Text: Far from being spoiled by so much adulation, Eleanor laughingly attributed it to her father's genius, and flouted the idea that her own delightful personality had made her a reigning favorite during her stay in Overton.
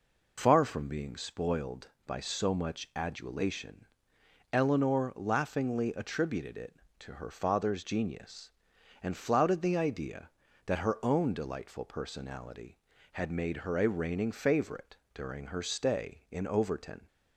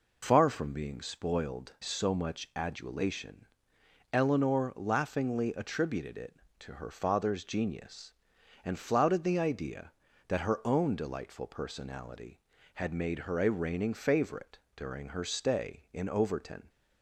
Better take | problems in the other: first | skips "by"; at 1.7 s // pauses between "favorite" and "during"; slight; at 14.5 s; 0.18 s long; slight in the first

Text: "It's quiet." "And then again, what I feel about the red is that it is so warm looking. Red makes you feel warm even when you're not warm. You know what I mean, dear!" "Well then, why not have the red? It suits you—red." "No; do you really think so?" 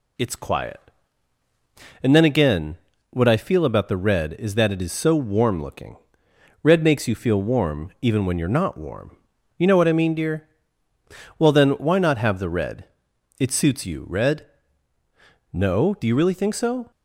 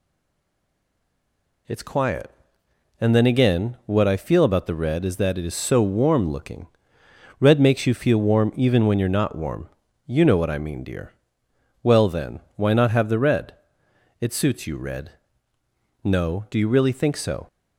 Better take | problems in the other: first | stays silent before the first word; noticeable; until 1.6 s; 1.6 s long

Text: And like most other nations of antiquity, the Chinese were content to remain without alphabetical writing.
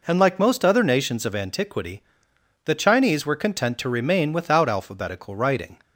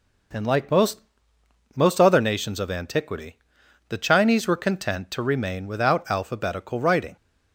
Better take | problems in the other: first | says "most" twice; at 1.7 s

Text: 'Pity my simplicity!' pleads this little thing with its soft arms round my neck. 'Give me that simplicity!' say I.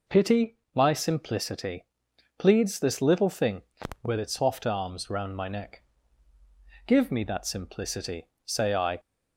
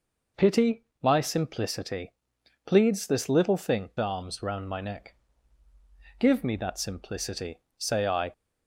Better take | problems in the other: first | pauses between "Pity" and "my"; slight; at 0.8 s; 0.16 s long; slight in the first // skips "with its soft"; at 3.9 s

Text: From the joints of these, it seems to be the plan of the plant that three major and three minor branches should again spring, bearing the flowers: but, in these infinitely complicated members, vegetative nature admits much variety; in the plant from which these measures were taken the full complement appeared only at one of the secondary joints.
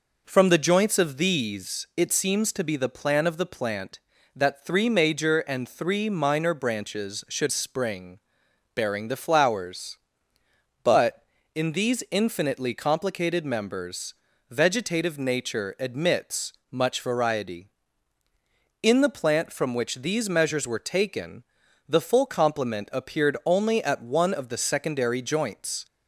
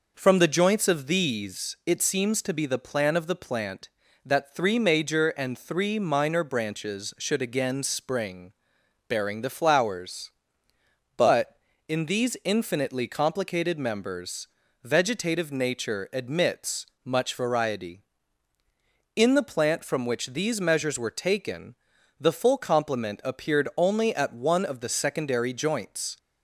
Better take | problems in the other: second | skips "again"; at 7.4 s // pauses between "admits" and "much"; slight; at 16.5 s; 0.18 s long; slight in the second // pauses between "taken" and "the"; noticeable; at 21.4 s; 0.46 s long; noticeable in the second

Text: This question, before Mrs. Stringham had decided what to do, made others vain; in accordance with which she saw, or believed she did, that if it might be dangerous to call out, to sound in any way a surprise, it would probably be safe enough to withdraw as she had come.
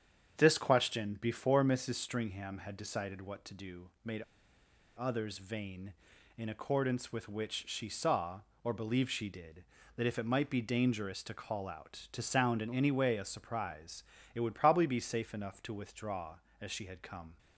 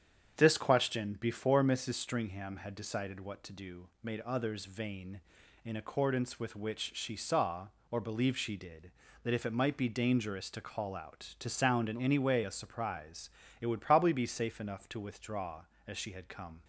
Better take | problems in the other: second | starts louder than the rest; strong; until 1.4 s; 8 dB; strong in the second // pauses between "made" and "others"; noticeable; at 4.2 s; 0.77 s long

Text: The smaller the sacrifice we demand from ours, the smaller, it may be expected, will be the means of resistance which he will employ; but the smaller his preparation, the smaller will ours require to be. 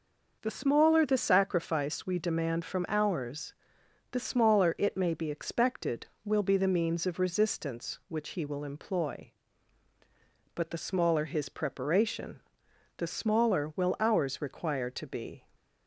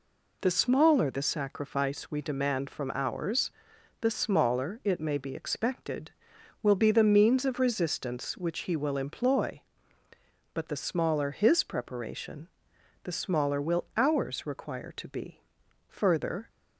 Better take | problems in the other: first | goes on to say "Further"; from 15.8 s on; 0.60 s long

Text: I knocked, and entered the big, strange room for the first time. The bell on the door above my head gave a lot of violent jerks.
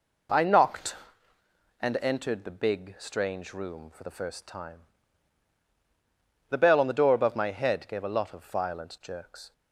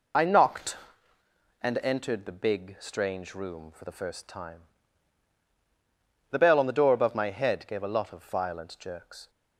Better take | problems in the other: first | loses the start of "I"; at 0.1 s; 45 ms

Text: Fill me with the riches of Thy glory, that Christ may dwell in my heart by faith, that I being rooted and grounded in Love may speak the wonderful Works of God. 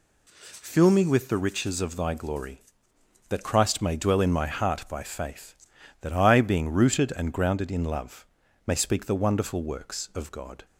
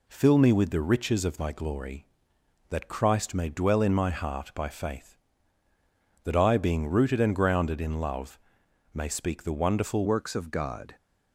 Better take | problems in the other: first | pauses between "Love" and "may"; noticeable; at 8.3 s; 0.56 s long; also in the first // changes voice at "Works"; from 10.0 s on; 0.9 s long

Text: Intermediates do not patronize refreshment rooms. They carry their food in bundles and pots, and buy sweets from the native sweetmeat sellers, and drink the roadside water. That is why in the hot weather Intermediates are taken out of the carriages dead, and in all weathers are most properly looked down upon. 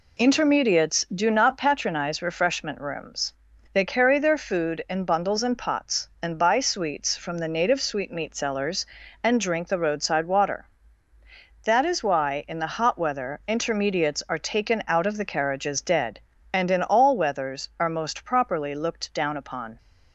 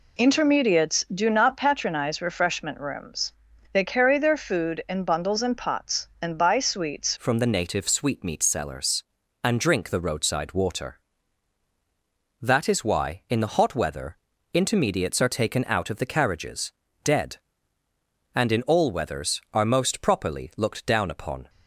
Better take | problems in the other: first | changes voice at "from"; from 7.1 s on; 14.3 s long // pauses between "weather" and "Intermediates"; slight; at 14.1 s; 0.36 s long // pauses between "carriages" and "dead"; slight; at 16.7 s; 0.32 s long

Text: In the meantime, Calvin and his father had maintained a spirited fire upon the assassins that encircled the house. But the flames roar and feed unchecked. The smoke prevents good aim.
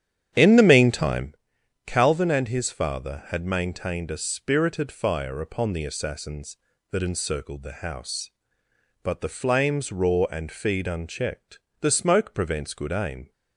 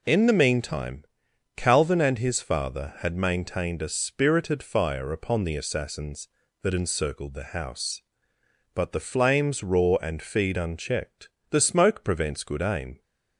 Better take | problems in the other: second | starts louder than the rest; strong; until 1.4 s; 10 dB

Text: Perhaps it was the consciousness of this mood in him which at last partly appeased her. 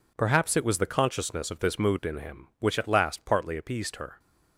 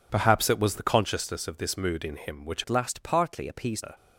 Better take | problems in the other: first | changes voice from "at" to "appeased"; from 2.6 to 3.8 s; 1.2 s long

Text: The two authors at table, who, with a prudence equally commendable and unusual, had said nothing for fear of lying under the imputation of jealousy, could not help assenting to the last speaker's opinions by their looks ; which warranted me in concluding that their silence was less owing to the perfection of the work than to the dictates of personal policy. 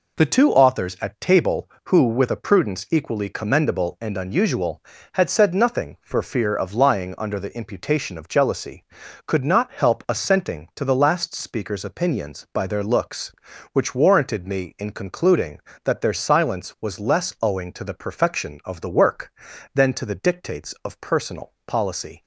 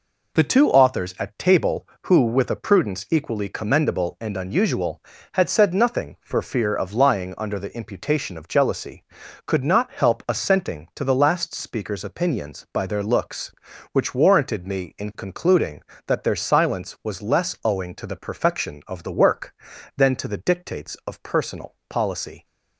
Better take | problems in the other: neither | none

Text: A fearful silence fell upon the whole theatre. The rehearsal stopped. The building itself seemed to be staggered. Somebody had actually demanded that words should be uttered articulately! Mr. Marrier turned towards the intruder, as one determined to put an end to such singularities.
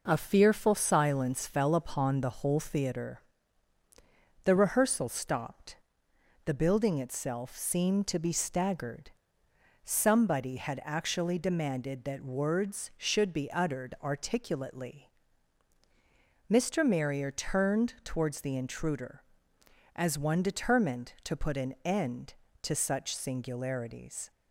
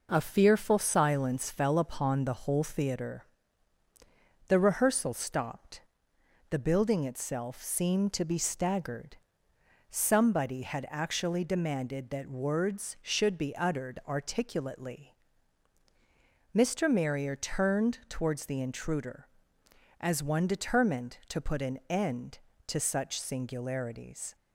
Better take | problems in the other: neither | none

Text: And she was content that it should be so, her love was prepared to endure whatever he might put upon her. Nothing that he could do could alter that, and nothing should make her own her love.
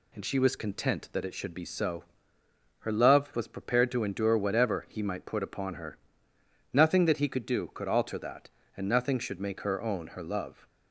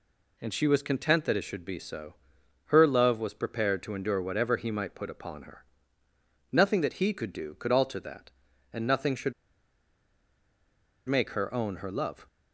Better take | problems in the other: first | pauses between "should" and "make"; strong; at 9.3 s; 1.7 s long

